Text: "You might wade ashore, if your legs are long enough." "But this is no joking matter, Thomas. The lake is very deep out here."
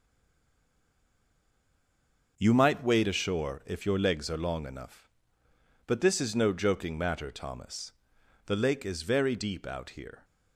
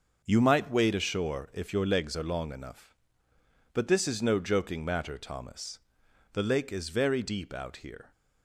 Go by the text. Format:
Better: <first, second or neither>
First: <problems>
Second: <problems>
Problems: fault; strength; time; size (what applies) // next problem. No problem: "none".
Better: second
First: stays silent before the first word; until 2.3 s; 2.3 s long // starts louder than the rest; until 3.3 s; 6 dB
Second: starts louder than the rest; until 1.2 s; 6 dB